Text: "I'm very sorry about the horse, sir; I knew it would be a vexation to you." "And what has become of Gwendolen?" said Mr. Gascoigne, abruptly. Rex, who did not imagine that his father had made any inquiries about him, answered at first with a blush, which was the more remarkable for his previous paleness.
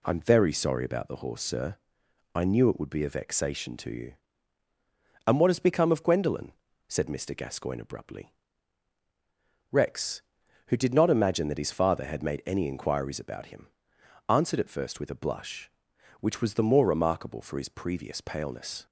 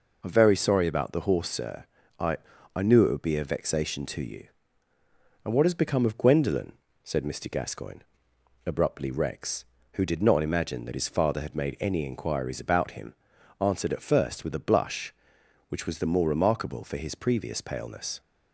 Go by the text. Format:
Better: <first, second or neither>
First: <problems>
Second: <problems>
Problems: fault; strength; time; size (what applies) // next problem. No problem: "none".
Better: first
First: none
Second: says "I" twice; at 2.7 s